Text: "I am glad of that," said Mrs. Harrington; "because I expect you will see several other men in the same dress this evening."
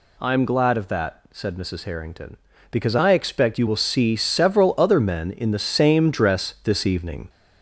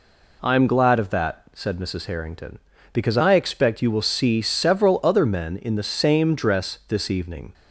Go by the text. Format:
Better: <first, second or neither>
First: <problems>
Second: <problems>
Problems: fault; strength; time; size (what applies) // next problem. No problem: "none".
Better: second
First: gets louder; throughout; 4 dB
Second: none